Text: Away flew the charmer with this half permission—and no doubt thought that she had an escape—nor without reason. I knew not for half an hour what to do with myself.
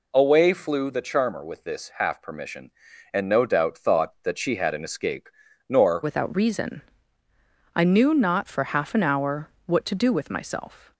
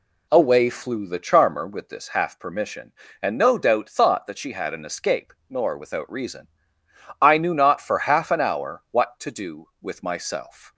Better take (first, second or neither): second